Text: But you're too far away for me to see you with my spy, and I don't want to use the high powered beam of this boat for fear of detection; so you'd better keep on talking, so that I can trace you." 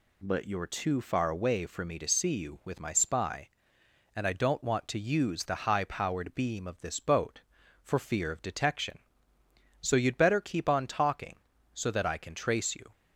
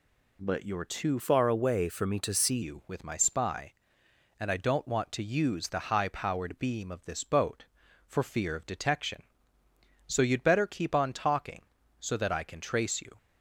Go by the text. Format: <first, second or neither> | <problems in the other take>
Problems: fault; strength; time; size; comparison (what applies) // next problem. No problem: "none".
first | changes voice from "far" to "see"; from 1.1 to 2.6 s; 1.5 s long